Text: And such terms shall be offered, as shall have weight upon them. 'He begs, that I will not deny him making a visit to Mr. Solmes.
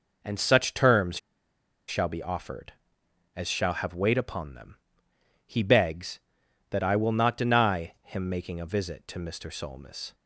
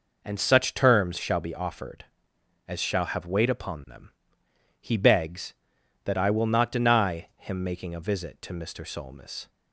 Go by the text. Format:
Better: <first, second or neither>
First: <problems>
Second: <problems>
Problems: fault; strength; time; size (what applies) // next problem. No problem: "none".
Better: second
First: pauses between "terms" and "shall"; noticeable; at 1.1 s; 0.70 s long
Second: none